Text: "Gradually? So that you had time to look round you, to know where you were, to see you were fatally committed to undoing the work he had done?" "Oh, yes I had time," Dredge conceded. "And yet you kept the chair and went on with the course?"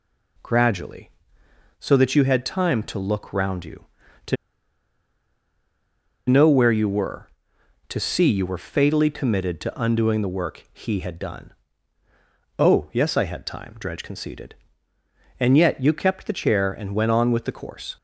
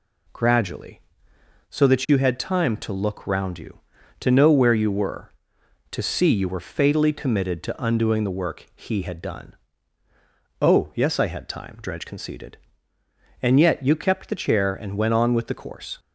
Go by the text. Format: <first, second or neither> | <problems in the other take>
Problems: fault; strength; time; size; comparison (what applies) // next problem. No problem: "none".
second | pauses between "to" and "know"; strong; at 4.3 s; 1.9 s long